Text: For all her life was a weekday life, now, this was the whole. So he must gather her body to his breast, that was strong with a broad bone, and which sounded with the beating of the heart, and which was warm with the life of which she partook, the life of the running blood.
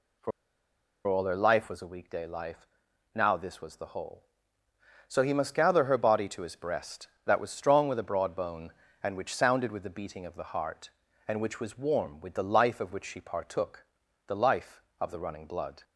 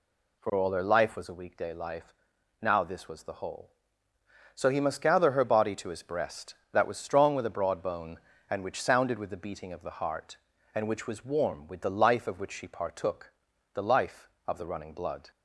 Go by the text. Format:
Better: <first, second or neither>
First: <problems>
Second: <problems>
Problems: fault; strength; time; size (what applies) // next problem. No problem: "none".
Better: second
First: pauses between "For" and "all"; noticeable; at 0.3 s; 0.76 s long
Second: none